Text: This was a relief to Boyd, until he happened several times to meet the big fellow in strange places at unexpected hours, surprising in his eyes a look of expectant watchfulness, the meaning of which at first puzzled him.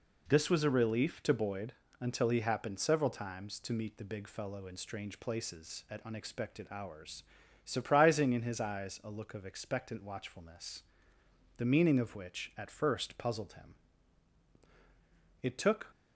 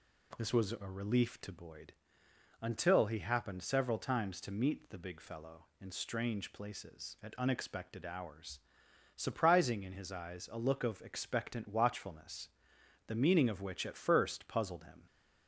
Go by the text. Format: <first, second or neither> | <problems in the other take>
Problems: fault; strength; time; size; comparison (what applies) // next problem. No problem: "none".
second | goes on to say "It took"; slight; from 15.4 s on; 0.48 s long